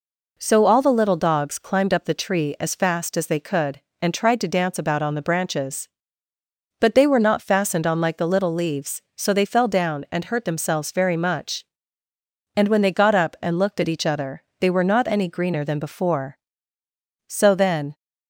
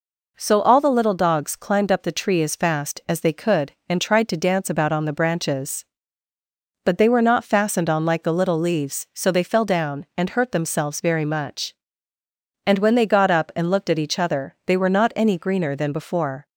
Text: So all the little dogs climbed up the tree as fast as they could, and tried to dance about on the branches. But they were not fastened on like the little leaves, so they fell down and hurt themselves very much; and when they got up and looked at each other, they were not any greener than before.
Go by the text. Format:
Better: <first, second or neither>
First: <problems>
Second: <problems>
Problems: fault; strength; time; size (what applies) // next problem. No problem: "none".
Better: second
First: goes on to say "So then"; noticeable; from 17.2 s on; 0.70 s long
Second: none